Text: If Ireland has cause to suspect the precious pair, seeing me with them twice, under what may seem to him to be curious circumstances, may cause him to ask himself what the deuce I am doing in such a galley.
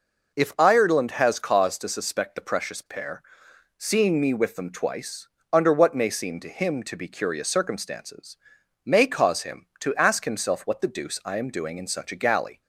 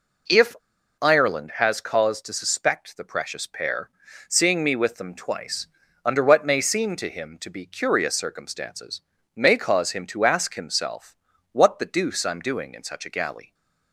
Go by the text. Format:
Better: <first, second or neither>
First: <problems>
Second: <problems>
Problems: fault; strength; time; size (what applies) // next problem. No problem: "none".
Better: first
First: none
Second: pauses between "If" and "Ireland"; at 0.5 s; 0.45 s long // pauses between "himself" and "what"; slight; at 11.1 s; 0.36 s long